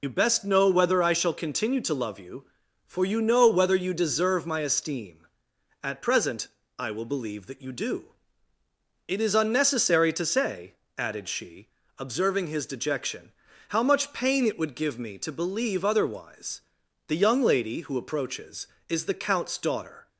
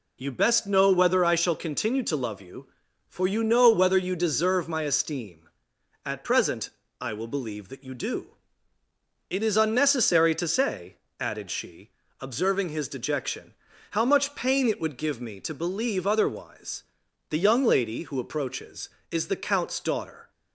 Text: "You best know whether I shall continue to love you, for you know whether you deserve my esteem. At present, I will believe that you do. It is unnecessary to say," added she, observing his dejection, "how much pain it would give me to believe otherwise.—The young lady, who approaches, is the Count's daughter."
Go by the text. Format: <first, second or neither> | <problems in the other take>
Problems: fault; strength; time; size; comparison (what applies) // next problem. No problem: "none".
second | loses the start of "You"; at 0.0 s; 50 ms